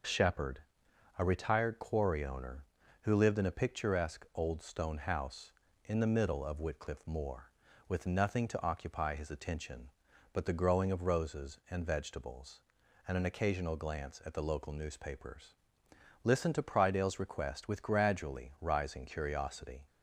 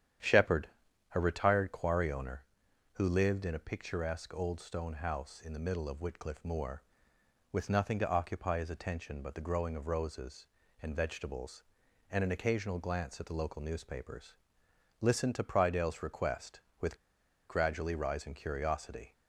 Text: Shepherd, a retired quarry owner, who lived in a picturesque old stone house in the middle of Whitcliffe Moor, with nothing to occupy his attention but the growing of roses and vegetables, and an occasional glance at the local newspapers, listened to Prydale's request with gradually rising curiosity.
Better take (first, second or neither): first